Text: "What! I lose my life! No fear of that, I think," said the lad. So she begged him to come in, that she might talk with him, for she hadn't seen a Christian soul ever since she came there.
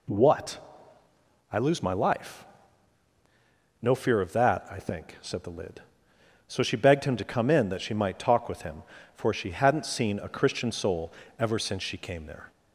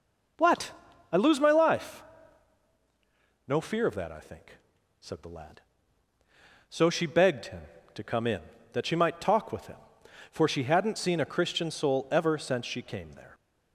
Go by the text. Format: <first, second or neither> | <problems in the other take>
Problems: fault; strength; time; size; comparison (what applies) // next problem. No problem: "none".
second | says "lid" for "lad"; at 5.5 s // pauses between "soul" and "ever"; slight; at 11.1 s; 0.26 s long